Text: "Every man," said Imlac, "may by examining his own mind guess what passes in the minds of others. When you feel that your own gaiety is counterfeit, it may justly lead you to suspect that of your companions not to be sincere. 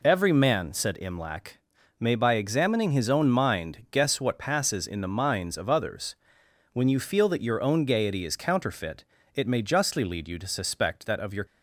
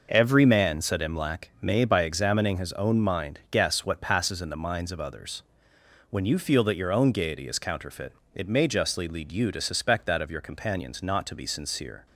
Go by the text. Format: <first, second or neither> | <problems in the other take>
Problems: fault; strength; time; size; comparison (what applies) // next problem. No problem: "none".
second | stops before "companions not to be sincere"; at 11.4 s